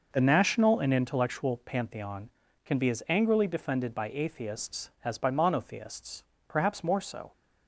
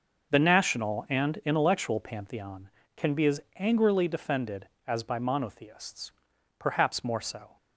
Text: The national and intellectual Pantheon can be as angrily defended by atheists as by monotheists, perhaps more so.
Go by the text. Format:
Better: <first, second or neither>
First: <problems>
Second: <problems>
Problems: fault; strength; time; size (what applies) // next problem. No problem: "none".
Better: first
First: none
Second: pauses between "as" and "angrily"; slight; at 3.4 s; 0.18 s long // skips "by atheists"; at 4.7 s